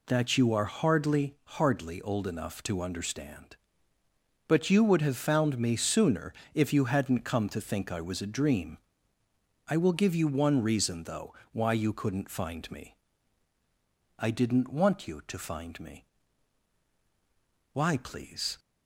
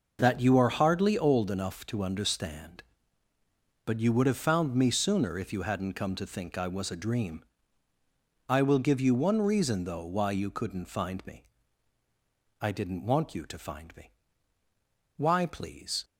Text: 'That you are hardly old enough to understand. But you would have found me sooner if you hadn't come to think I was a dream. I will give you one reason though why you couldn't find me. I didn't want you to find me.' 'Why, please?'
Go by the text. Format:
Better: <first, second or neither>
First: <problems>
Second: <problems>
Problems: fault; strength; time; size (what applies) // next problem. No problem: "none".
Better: second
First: says "hardly" twice; at 1.4 s // pauses between "sooner" and "if"; slight; at 6.3 s; 0.20 s long // pauses between "though" and "why"; slight; at 11.3 s; 0.20 s long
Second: none